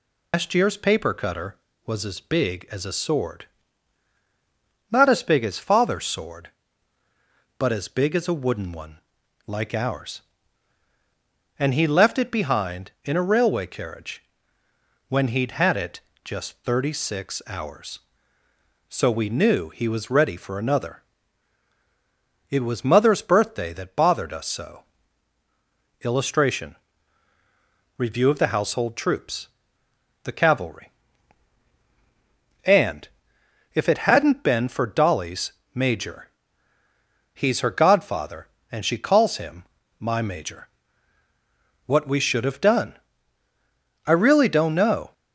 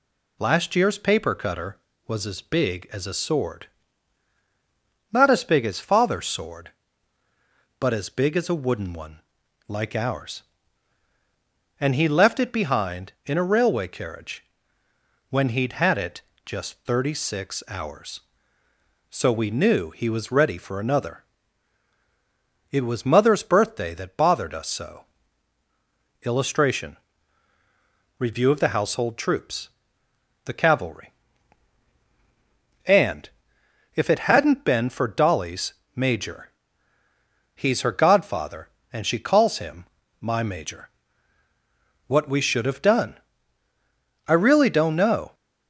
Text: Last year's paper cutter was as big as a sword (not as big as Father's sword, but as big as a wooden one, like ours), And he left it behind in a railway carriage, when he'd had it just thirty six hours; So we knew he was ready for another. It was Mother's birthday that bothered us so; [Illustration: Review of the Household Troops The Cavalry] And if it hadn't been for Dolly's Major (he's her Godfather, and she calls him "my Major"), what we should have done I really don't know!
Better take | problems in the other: second | loses the start of "Last"; at 0.3 s; 150 ms // pauses between "it" and "just"; slight; at 16.0 s; 0.24 s long; slight in the second // pauses between "Troops" and "The"; noticeable; at 29.4 s; 0.78 s long; noticeable in the second // pauses between "And" and "if"; noticeable; at 33.0 s; 0.66 s long; noticeable in the second // pauses between "Dolly's" and "Major"; slight; at 35.5 s; 0.20 s long; slight in the second // pauses between "him" and "my"; slight; at 39.6 s; 0.34 s long; slight in the second // pauses between "done" and "I"; at 42.9 s; 1.1 s long; also in the second

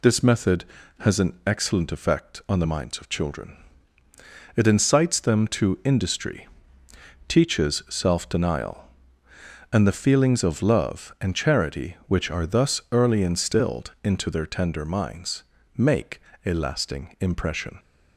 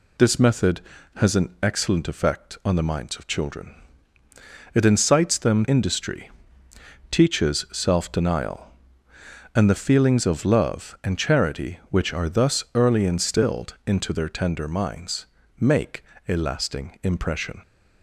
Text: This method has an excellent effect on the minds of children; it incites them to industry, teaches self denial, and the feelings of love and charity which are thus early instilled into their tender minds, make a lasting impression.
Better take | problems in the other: first | skips "to"; at 5.6 s // pauses between "make" and "a"; slight; at 16.0 s; 0.24 s long; slight in the first

